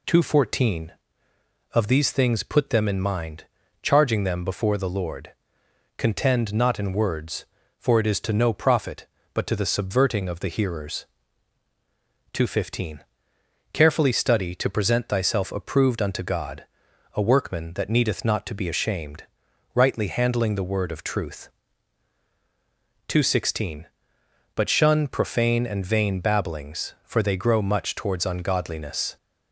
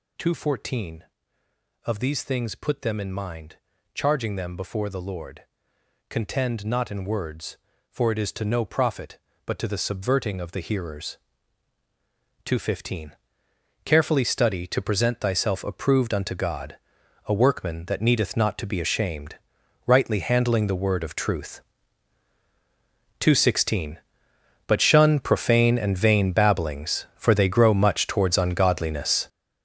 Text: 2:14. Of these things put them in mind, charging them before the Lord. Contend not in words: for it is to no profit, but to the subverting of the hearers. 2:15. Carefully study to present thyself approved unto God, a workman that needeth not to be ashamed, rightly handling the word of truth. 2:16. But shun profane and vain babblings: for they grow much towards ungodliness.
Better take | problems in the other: first | gets louder; strong; throughout; 10.5 dB

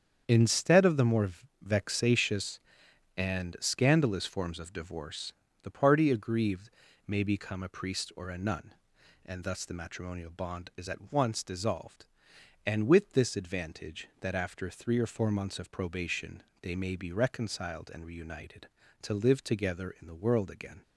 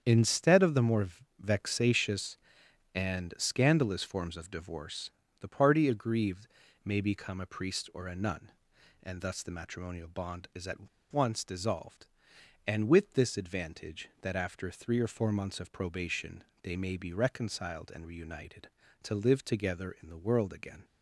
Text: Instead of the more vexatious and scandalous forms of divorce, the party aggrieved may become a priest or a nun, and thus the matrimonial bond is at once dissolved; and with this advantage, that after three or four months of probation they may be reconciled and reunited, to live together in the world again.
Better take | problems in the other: first | starts louder than the rest; strong; until 1.0 s; 8 dB; strong in the first // pauses between "more" and "vexatious"; slight; at 1.0 s; 0.32 s long; slight in the first // pauses between "aggrieved" and "may"; at 6.4 s; 0.38 s long; also in the first // pauses between "at" and "once"; slight; at 10.8 s; 0.23 s long // pauses between "probation" and "they"; slight; at 16.4 s; 0.18 s long; slight in the first

